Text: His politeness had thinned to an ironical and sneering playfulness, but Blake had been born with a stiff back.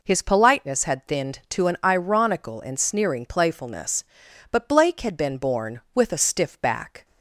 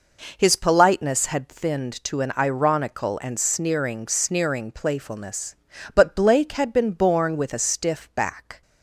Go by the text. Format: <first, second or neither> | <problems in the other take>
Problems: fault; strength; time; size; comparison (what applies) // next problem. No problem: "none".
first | says "sneering" twice; at 4.0 s